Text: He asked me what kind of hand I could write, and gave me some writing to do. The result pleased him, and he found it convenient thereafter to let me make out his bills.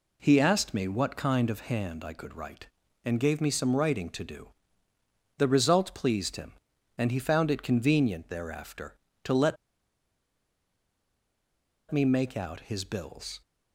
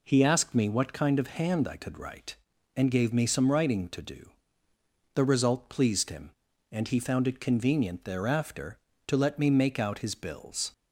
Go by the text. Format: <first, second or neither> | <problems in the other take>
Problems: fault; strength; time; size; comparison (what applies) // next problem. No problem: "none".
second | pauses between "let" and "me"; strong; at 9.5 s; 2.3 s long